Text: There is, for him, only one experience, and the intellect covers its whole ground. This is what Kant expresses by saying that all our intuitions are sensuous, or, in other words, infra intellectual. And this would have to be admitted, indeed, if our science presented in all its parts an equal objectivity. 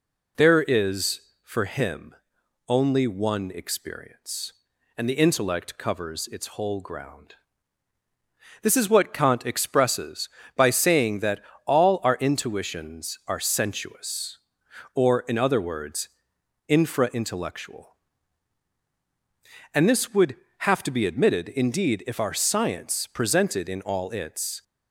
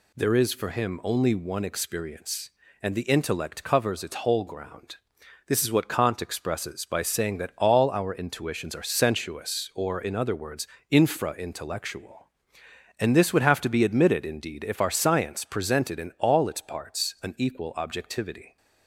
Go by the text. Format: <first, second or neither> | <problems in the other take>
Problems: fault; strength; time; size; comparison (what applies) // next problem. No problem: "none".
second | pauses between "that" and "all"; slight; at 11.4 s; 0.24 s long // stops before "parts an equal objectivity"; at 24.6 s